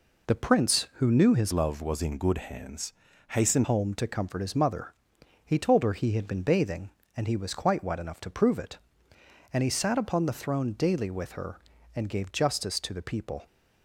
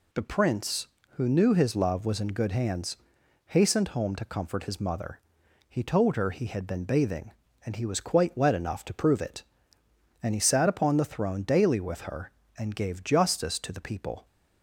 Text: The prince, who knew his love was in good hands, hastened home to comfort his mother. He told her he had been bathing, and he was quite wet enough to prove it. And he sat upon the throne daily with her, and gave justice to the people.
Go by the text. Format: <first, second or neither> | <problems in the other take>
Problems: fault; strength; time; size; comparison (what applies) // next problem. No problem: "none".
second | changes voice from "love" to "hastened"; from 1.5 to 3.6 s; 2.1 s long